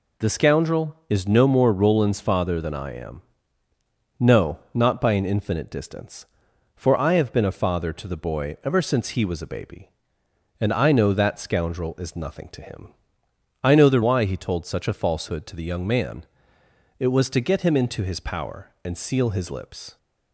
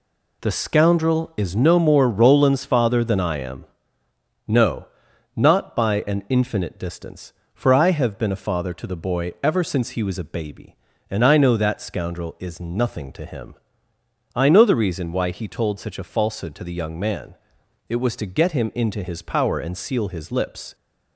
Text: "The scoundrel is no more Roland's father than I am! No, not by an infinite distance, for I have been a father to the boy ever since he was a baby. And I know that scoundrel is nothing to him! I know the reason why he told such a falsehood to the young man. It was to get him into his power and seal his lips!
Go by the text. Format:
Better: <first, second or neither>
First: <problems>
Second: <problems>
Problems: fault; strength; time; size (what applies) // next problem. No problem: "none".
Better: second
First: skips "reason"; at 14.0 s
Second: none